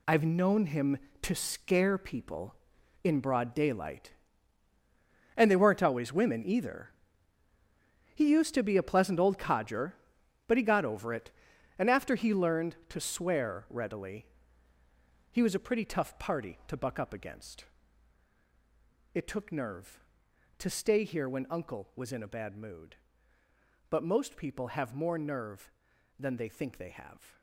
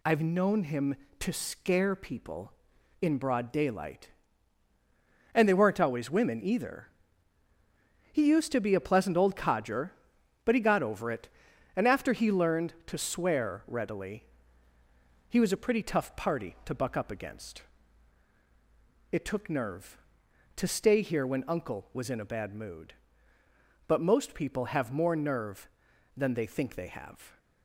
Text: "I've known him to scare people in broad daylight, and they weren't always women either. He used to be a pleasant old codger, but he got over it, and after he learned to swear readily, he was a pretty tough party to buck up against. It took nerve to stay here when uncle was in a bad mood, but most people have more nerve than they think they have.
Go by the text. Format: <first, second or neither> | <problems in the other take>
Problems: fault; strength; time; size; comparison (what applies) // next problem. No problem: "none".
second | gets quieter; strong; throughout; 11 dB